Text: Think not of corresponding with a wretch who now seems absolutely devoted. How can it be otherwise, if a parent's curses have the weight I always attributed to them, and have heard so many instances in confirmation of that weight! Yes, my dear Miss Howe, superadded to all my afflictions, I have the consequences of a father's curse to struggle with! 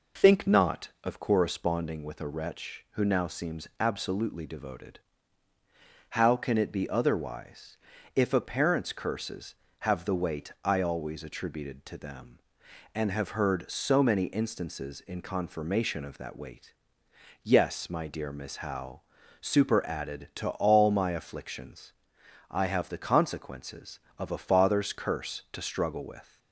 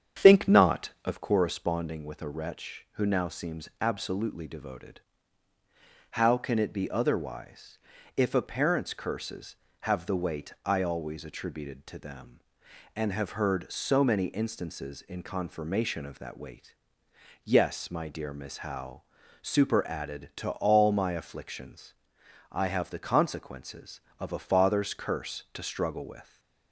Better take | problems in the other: first | starts louder than the rest; strong; until 1.3 s; 8.5 dB

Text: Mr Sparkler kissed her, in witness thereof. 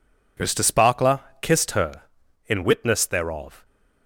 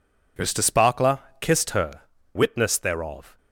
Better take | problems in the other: first | pauses between "Sparkler" and "kissed"; slight; at 1.1 s; 0.24 s long; slight in the first // skips "in"; at 2.1 s

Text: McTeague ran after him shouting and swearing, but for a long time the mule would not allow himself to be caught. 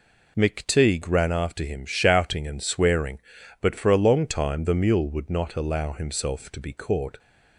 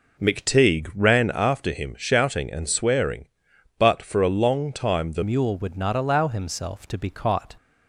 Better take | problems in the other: first | changes voice at "mule"; from 5.2 s on; 2.3 s long

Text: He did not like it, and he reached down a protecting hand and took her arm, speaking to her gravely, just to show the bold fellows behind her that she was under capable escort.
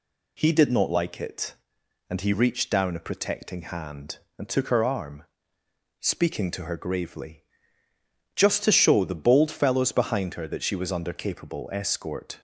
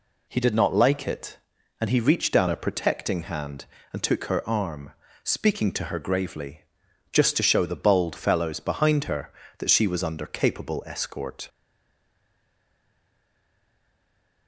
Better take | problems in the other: first | stays silent after the last word; strong; from 11.4 s on; 3.0 s long

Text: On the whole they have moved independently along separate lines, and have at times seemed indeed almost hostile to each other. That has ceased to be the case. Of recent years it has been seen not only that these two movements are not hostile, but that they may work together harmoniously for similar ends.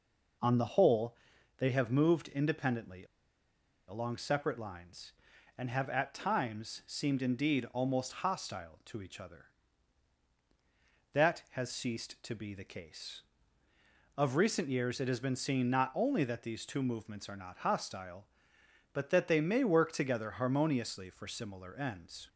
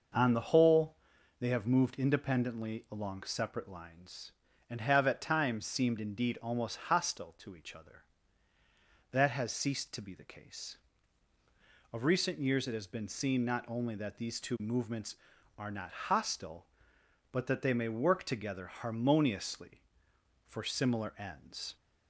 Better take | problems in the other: second | pauses between "whole" and "they"; at 1.1 s; 0.44 s long; also in the second // pauses between "independently" and "along"; noticeable; at 3.0 s; 0.82 s long

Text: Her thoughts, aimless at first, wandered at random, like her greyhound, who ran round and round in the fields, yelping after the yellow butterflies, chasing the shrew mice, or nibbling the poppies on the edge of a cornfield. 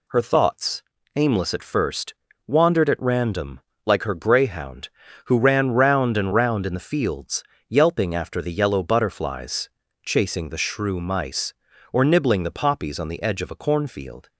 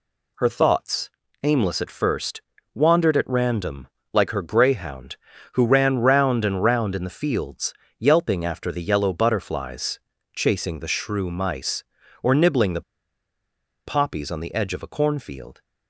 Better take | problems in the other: first | pauses between "the" and "poppies"; at 12.8 s; 1.0 s long

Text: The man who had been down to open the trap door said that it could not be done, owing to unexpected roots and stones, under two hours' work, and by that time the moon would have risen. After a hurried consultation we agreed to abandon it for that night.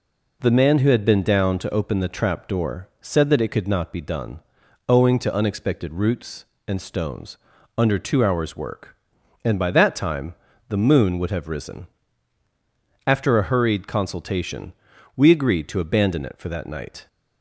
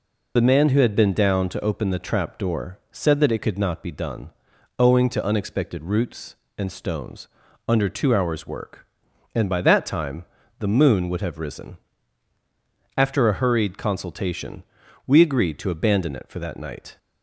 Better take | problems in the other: first | loses the start of "The"; at 0.3 s; 40 ms // pauses between "time" and "the"; slight; at 10.2 s; 0.36 s long; slight in the first // pauses between "consultation" and "we"; noticeable; at 14.6 s; 0.46 s long; noticeable in the first

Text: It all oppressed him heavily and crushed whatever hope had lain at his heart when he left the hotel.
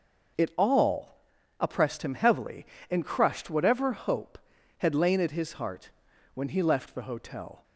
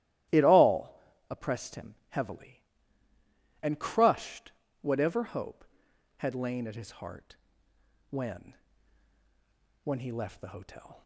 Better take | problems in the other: first | starts louder than the rest; strong; until 1.6 s; 15 dB // pauses between "all" and "oppressed"; slight; at 1.0 s; 0.30 s long; also in the first // pauses between "him" and "heavily"; slight; at 1.9 s; 0.16 s long // pauses between "crushed" and "whatever"; slight; at 4.5 s; 0.30 s long // pauses between "heart" and "when"; noticeable; at 7.3 s; 0.74 s long; also in the first // says "when" twice; at 9.8 s

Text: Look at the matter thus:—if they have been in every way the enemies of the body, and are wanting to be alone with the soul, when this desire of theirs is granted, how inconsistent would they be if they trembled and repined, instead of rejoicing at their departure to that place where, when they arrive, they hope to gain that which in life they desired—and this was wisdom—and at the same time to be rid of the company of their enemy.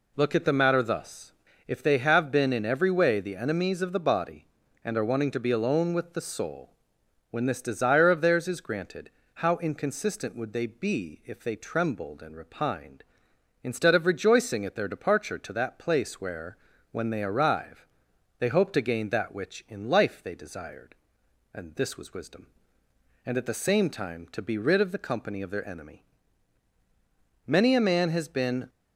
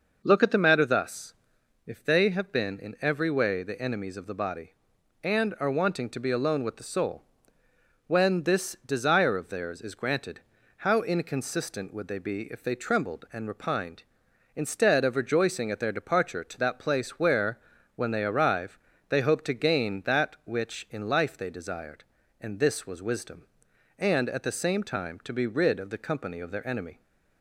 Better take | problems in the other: second | goes on to say "Many a man has been"; noticeable; from 27.4 s on; 1.2 s long

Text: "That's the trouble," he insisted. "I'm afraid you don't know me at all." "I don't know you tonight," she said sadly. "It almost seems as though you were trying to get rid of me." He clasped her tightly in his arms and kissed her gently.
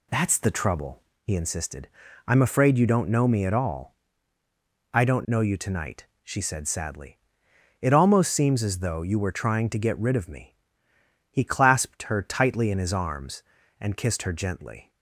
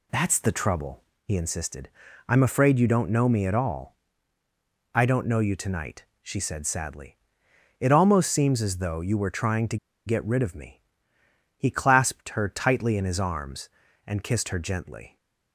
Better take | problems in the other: first | pauses between "to" and "get"; slight; at 9.7 s; 0.29 s long

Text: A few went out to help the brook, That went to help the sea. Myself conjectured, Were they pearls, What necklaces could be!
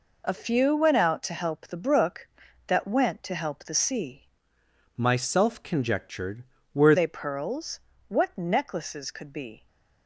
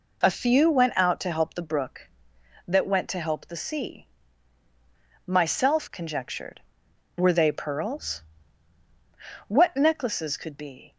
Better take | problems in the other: second | changes voice from "Myself" to "Were"; from 4.9 to 6.9 s; 2.0 s long

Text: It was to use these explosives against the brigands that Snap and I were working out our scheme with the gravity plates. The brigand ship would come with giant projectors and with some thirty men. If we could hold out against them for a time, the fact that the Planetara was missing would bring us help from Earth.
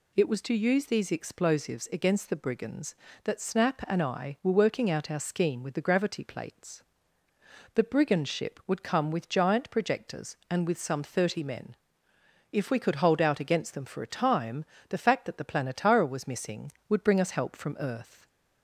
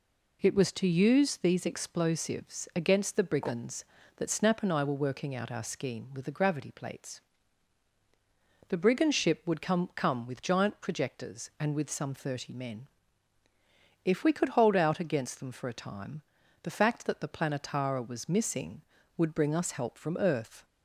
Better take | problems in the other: first | says "come" twice; at 9.9 s

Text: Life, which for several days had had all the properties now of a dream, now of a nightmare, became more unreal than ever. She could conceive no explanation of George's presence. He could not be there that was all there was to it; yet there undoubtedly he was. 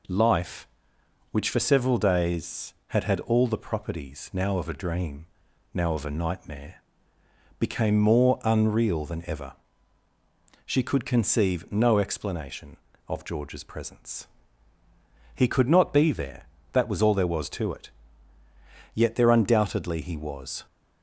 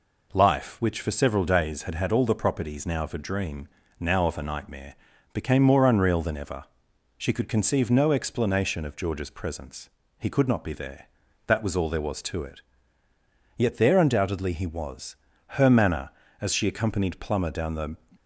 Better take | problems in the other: first | goes on to say "Her manner as she accompanied Plummer down the"; strong; from 15.5 s on; 2.4 s long

